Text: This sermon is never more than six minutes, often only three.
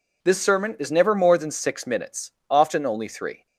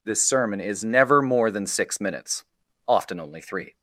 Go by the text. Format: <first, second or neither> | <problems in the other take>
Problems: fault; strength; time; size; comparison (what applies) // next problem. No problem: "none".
neither | none